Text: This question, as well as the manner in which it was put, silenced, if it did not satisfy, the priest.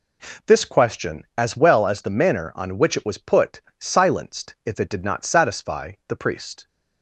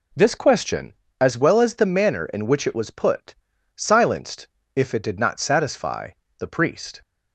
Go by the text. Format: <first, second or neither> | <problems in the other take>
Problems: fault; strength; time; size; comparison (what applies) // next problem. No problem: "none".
second | says "on" for "in"; at 2.5 s